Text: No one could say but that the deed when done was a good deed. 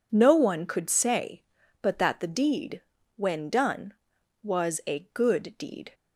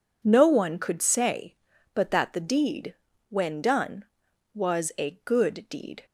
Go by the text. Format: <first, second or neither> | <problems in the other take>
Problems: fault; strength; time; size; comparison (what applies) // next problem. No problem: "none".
neither | pauses between "deed" and "when"; slight; the same in both